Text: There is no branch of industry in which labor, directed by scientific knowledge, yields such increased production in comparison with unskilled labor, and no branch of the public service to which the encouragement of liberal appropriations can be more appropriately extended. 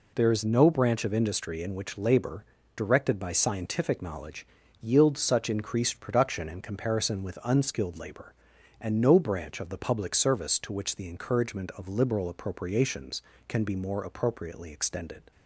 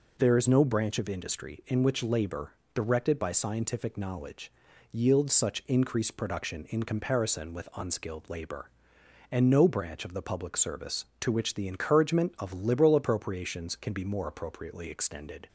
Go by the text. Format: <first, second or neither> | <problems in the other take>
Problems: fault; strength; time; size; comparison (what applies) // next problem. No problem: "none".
neither | none